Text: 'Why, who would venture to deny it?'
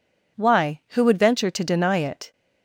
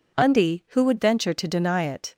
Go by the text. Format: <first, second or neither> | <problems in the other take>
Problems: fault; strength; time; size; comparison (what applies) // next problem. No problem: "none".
first | says "Undy" for "Why"; at 0.1 s